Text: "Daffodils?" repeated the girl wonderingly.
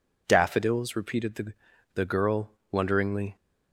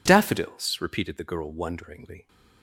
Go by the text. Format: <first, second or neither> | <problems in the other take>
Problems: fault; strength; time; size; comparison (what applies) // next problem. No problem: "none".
second | says "the" twice; at 1.9 s // pauses between "girl" and "wonderingly"; slight; at 2.5 s; 0.16 s long